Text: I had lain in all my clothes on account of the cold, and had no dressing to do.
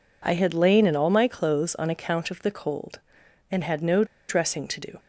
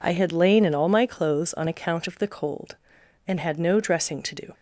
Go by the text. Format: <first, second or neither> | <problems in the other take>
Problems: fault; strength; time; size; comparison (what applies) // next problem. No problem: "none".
second | pauses between "no" and "dressing"; slight; at 4.0 s; 0.23 s long